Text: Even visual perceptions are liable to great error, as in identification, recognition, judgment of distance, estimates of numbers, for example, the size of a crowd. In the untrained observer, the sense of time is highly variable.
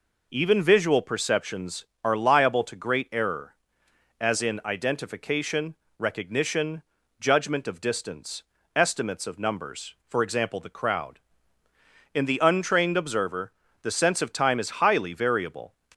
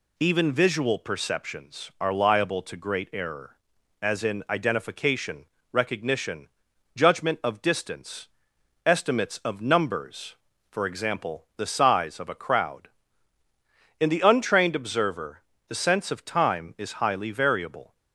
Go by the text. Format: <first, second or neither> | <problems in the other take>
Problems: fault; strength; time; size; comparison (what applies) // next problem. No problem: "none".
second | skips "size of a"; at 10.6 s